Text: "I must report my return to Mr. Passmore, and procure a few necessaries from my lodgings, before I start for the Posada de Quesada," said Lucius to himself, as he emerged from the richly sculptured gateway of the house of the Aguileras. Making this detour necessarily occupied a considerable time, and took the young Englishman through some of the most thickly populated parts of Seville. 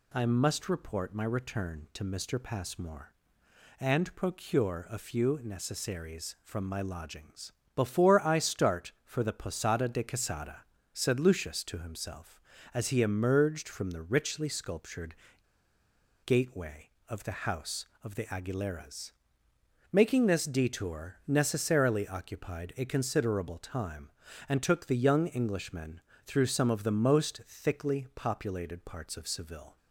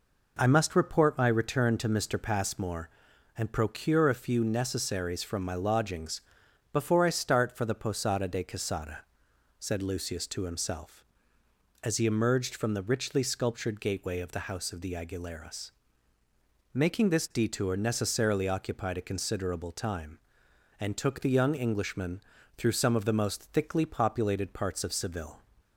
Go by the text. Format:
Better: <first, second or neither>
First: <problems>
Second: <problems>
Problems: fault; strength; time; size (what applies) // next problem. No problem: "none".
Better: second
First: pauses between "sculptured" and "gateway"; at 15.1 s; 1.1 s long // pauses between "Englishman" and "through"; slight; at 26.0 s; 0.26 s long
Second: pauses between "Englishman" and "through"; slight; at 22.2 s; 0.34 s long